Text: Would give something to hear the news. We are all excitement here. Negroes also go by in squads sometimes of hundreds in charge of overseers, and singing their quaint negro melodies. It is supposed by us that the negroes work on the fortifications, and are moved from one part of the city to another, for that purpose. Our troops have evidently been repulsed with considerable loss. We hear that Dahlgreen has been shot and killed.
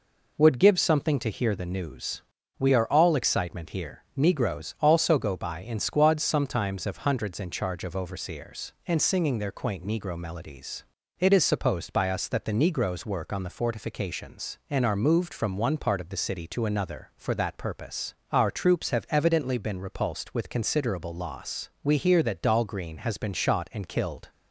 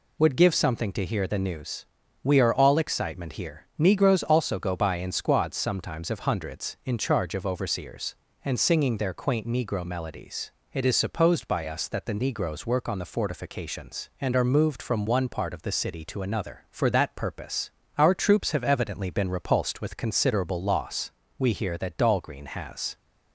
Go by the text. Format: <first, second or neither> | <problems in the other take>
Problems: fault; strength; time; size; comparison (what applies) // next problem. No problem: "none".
first | stops before "been shot and killed"; at 22.9 s